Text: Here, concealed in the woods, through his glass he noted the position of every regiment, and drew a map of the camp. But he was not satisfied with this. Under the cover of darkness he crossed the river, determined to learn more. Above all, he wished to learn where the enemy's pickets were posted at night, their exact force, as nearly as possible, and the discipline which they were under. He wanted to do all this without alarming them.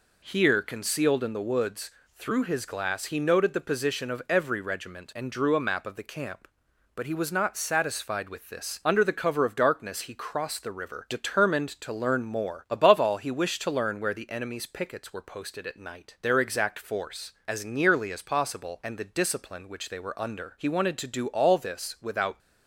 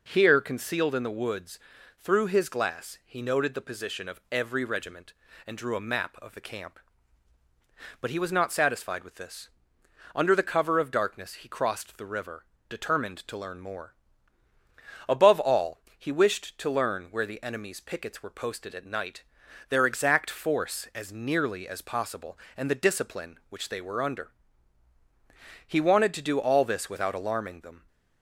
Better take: second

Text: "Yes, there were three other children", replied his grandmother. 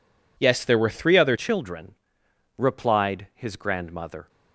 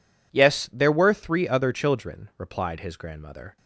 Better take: second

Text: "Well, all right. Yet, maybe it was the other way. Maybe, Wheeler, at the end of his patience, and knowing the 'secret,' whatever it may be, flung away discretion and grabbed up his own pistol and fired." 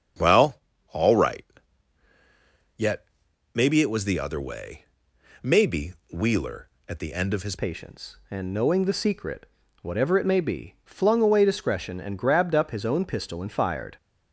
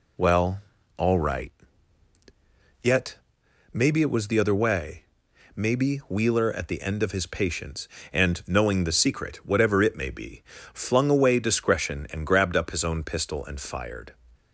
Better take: second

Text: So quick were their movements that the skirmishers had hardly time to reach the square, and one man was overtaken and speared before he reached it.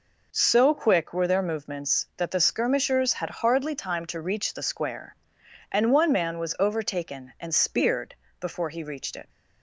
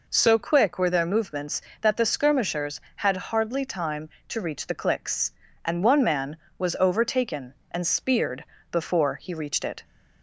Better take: first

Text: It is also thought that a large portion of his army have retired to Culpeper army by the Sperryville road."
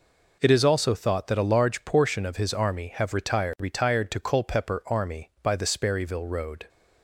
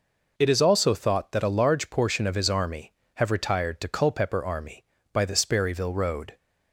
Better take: second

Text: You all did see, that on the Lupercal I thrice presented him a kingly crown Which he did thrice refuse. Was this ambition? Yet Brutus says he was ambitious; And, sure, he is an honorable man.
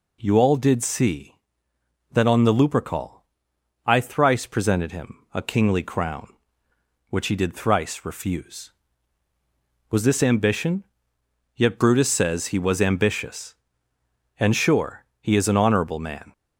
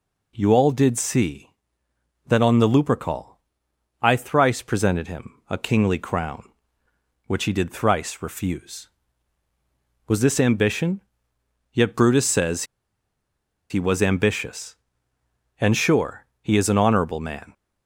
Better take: first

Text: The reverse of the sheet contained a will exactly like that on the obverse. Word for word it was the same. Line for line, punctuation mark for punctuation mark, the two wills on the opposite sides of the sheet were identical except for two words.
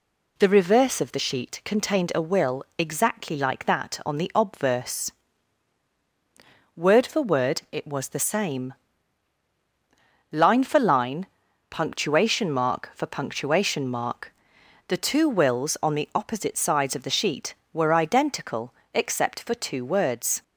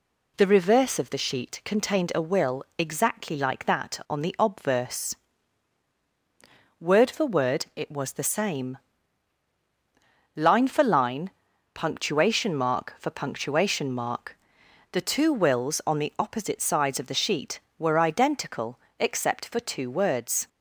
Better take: neither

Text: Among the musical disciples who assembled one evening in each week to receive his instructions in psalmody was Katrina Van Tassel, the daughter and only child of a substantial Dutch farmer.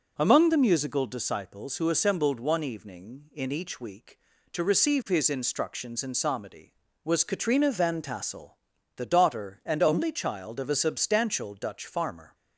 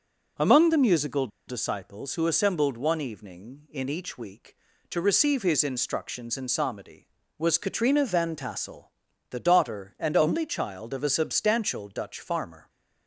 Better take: first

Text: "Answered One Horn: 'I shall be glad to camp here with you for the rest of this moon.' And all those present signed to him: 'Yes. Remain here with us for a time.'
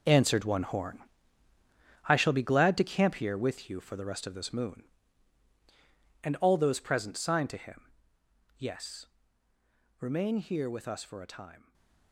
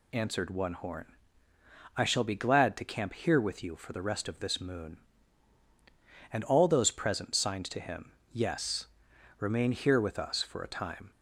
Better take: second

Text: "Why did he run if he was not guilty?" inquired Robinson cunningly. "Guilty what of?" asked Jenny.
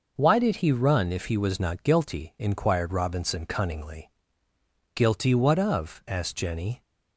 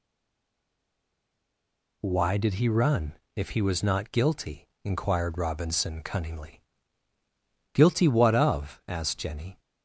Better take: first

